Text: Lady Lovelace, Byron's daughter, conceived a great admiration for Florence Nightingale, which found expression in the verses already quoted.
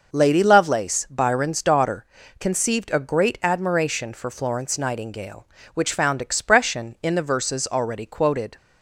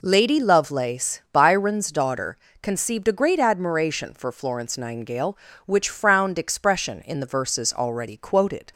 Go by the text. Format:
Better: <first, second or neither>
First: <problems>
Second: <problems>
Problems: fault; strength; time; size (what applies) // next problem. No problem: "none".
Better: first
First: none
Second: says "frowned" for "found"; at 5.8 s